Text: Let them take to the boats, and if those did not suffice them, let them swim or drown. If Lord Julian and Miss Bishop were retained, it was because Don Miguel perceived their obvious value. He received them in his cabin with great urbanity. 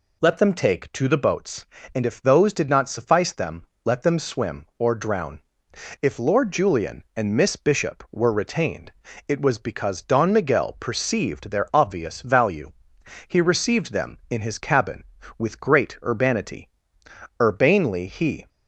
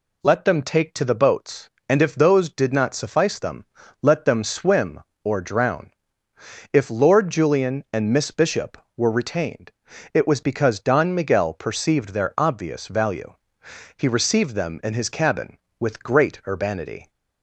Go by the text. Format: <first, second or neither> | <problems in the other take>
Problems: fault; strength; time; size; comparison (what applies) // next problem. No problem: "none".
second | goes on to say "Urbanely he"; noticeable; from 17.4 s on; 1.0 s long